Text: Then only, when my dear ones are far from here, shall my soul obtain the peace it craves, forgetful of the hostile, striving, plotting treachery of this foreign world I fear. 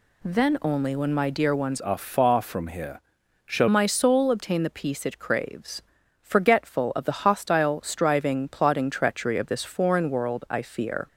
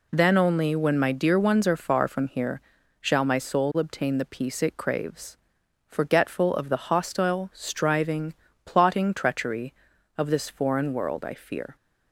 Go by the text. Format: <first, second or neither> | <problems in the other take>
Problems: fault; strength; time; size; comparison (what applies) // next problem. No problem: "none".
second | changes voice from "are" to "shall"; from 1.8 to 3.6 s; 1.8 s long